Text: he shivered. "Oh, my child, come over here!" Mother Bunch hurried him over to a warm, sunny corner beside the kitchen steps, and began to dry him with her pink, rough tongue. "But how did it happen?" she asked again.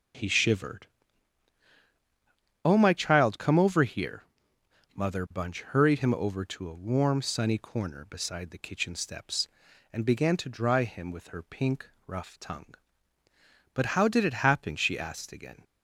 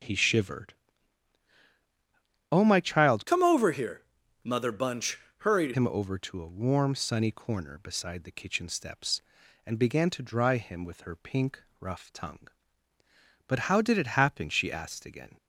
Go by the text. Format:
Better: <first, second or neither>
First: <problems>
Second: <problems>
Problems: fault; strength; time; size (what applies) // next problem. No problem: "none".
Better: first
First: none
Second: changes voice from "come" to "hurried"; from 3.2 to 5.7 s; 2.5 s long // pauses between "Bunch" and "hurried"; slight; at 5.1 s; 0.20 s long